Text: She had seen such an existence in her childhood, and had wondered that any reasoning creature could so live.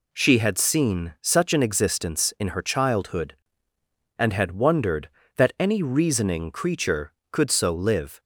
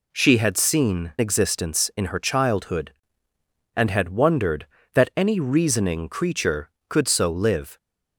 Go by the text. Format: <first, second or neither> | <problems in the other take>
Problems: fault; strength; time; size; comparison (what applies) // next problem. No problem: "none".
first | skips "such an"; at 1.1 s